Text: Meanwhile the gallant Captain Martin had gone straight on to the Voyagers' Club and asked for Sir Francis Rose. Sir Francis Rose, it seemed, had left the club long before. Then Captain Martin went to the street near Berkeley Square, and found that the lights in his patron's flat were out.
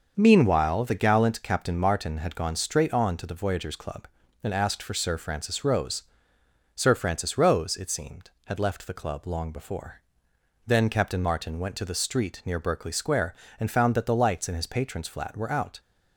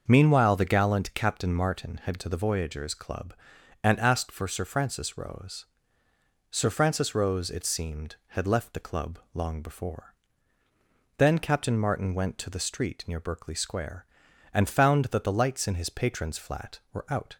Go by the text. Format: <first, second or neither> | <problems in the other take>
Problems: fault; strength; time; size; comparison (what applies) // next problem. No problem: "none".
first | starts louder than the rest; until 1.0 s; 6 dB; also in the first // skips "gone straight on"; at 2.2 s // pauses between "club" and "long"; slight; at 9.1 s; 0.16 s long